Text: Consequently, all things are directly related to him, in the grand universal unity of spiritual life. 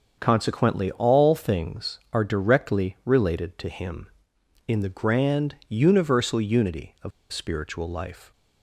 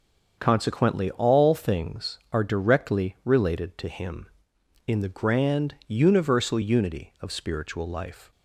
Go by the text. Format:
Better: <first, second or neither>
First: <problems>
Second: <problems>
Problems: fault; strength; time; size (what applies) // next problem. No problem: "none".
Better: second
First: starts louder than the rest; until 1.2 s; 6.5 dB // pauses between "of" and "spiritual"; slight; at 7.1 s; 0.21 s long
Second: starts louder than the rest; until 1.4 s; 6.5 dB